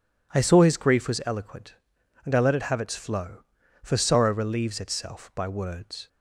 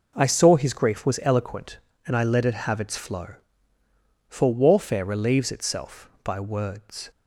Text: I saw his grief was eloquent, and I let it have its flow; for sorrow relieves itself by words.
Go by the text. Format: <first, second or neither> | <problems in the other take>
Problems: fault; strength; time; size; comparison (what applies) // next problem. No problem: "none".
first | says "warfare" for "sorrow"; at 4.5 s